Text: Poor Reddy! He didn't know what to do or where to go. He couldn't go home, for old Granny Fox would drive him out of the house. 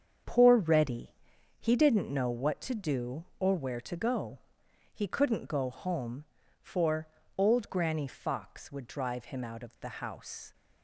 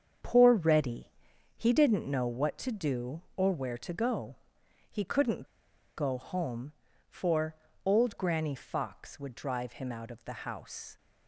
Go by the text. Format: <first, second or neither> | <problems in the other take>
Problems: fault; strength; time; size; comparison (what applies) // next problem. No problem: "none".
first | starts louder than the rest; strong; until 1.6 s; 7 dB; strong in the first // pauses between "couldn't" and "go"; noticeable; at 5.4 s; 0.53 s long // pauses between "for" and "old"; slight; at 7.5 s; 0.30 s long; slight in the first